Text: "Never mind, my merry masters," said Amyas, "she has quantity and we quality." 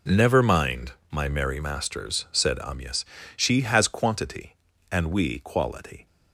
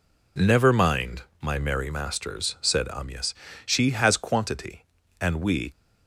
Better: first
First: none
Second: stops before "quality"; at 5.7 s

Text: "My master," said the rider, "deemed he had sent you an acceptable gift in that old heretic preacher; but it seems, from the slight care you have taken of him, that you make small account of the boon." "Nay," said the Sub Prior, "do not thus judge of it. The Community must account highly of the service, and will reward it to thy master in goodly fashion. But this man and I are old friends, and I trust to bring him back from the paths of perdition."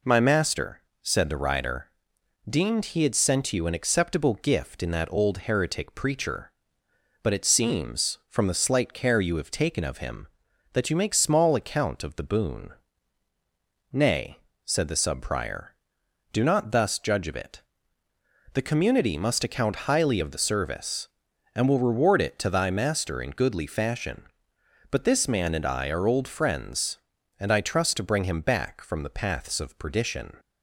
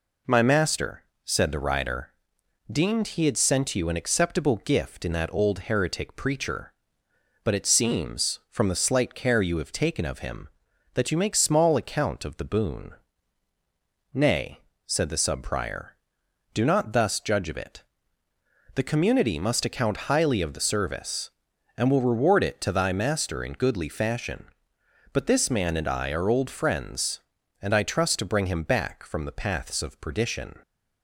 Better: neither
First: none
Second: none

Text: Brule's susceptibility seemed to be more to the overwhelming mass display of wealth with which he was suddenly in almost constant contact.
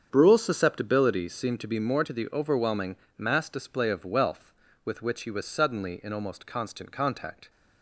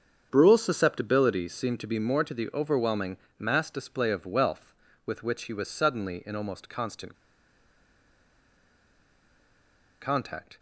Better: first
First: starts louder than the rest; strong; until 1.1 s; 8 dB // pauses between "overwhelming" and "mass"; slight; at 2.9 s; 0.20 s long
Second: starts louder than the rest; strong; until 1.3 s; 7.5 dB // pauses between "overwhelming" and "mass"; slight; at 3.1 s; 0.20 s long // pauses between "constant" and "contact"; strong; at 7.1 s; 2.8 s long

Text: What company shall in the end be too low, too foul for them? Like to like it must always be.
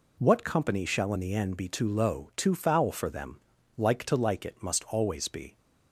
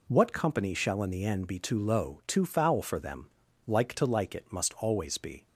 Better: neither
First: none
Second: none

